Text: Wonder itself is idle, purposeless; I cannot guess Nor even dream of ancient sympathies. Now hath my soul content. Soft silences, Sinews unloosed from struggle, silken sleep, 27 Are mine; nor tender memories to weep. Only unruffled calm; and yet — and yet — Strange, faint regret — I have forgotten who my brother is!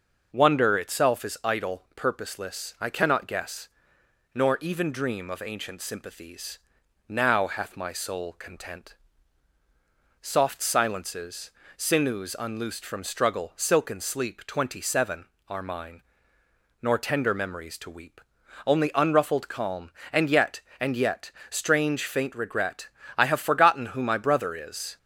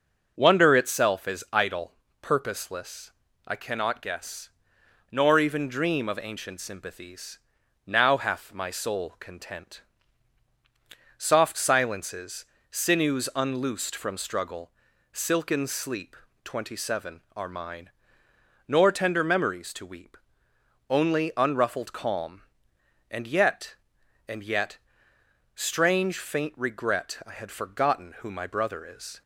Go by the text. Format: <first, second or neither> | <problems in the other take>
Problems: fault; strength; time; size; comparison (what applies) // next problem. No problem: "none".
first | pauses between "guess" and "Nor"; noticeable; at 4.4 s; 0.60 s long; noticeable in the first // says "had" for "have"; at 27.3 s